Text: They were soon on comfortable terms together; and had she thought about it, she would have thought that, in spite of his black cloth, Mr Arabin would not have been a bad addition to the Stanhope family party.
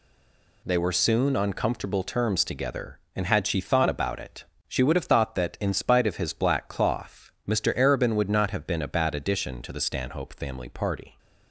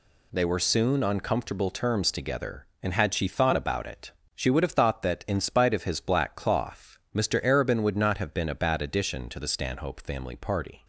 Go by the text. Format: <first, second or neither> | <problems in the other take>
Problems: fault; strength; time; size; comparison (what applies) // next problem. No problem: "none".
second | stays silent before the first word; slight; until 0.6 s; 0.6 s long